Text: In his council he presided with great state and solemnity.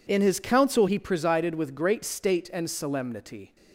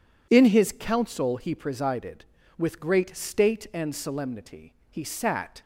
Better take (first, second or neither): first